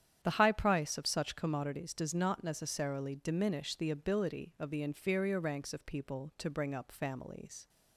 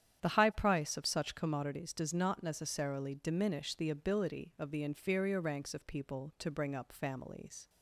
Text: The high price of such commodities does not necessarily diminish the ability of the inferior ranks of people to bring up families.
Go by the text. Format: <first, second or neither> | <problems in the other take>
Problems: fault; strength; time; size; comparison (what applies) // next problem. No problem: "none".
neither | starts louder than the rest; strong; the same in both